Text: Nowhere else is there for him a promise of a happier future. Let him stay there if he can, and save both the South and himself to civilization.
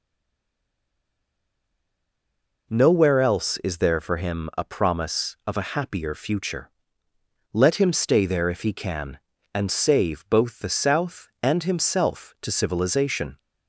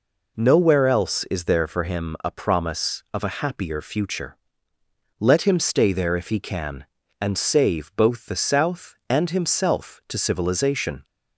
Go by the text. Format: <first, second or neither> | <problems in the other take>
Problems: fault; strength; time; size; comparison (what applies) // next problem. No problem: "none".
second | stays silent before the first word; strong; until 2.6 s; 2.6 s long